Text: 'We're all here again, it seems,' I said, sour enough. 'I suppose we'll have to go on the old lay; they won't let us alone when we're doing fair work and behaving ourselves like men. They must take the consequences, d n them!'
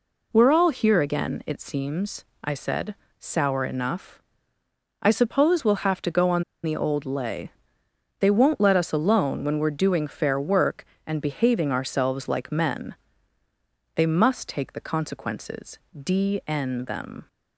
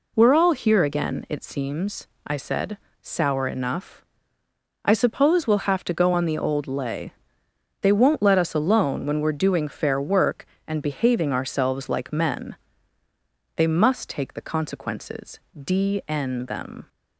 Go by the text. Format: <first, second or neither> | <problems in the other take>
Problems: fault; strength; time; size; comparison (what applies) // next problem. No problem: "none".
second | pauses between "on" and "the"; slight; at 6.4 s; 0.20 s long